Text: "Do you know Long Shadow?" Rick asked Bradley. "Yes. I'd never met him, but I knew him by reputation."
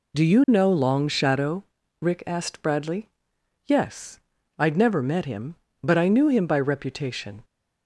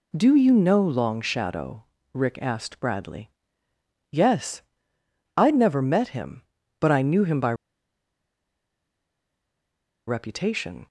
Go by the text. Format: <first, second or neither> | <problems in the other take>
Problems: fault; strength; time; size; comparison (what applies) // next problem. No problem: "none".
first | pauses between "by" and "reputation"; strong; at 7.5 s; 2.5 s long